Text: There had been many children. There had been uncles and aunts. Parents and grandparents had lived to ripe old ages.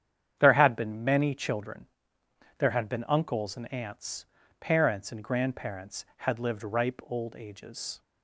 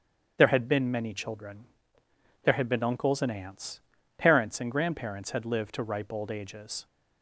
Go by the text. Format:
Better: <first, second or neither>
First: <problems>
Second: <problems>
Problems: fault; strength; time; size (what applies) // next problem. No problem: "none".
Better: second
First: starts louder than the rest; strong; until 1.3 s; 9 dB // skips "to"; at 6.6 s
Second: starts louder than the rest; strong; until 1.3 s; 8 dB